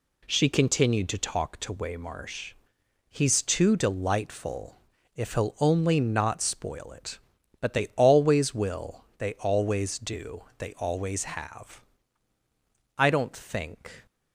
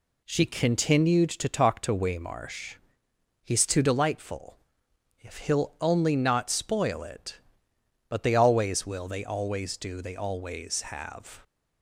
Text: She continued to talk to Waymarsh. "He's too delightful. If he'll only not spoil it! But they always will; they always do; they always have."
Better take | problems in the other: second | goes on to say "I don't think"; noticeable; from 12.9 s on; 1.1 s long

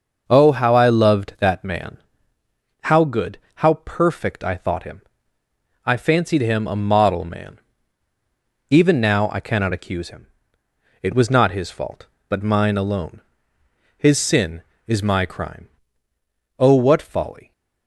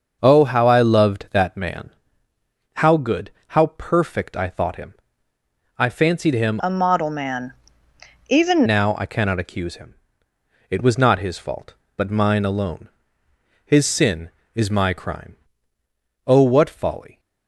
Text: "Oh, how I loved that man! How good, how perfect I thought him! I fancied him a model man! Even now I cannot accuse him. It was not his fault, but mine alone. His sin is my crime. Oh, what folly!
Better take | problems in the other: first | starts louder than the rest; until 1.2 s; 6 dB; also in the first // changes voice from "a" to "Even"; from 6.5 to 8.6 s; 2.1 s long

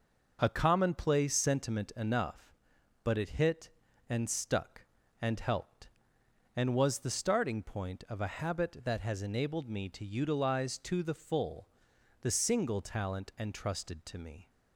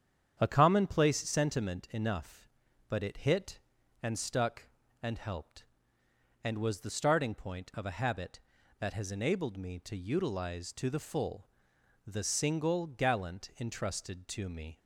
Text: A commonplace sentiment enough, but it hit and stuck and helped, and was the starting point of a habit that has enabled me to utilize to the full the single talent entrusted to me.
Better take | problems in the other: first | starts louder than the rest; strong; until 1.4 s; 8.5 dB // pauses between "full" and "the"; noticeable; at 11.4 s; 0.58 s long; noticeable in the first // says "gallant" for "talent"; at 12.8 s

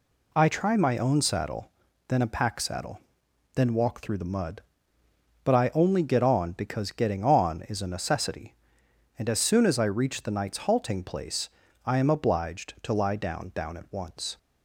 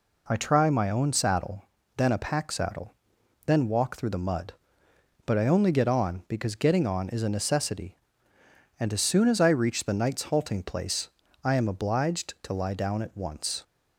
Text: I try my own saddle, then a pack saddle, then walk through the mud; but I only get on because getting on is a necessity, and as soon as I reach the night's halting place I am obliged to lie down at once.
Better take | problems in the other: second | pauses between "place" and "I"; slight; at 11.4 s; 0.36 s long; slight in the second // says "down" twice; at 13.5 s

